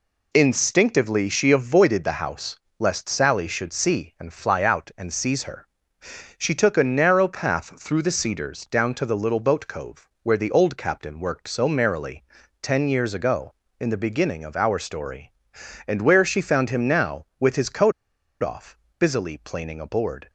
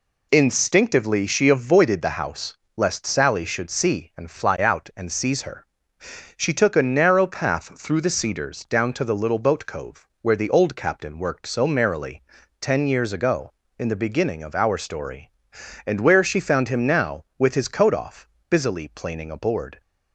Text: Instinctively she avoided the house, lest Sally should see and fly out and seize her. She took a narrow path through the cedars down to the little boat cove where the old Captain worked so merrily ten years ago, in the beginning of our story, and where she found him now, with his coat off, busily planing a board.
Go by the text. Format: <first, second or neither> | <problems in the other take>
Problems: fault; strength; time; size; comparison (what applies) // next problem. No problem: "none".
second | pauses between "cove" and "where"; slight; at 10.0 s; 0.16 s long; slight in the second // pauses between "merrily" and "ten"; at 12.2 s; 0.38 s long; also in the second // pauses between "coat" and "off"; noticeable; at 17.9 s; 0.49 s long